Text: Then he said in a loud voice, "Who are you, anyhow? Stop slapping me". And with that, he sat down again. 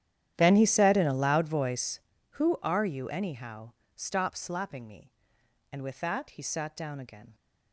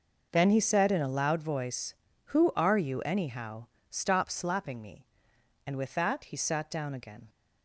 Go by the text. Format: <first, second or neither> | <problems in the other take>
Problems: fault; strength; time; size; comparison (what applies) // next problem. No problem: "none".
second | starts louder than the rest; strong; until 2.2 s; 11 dB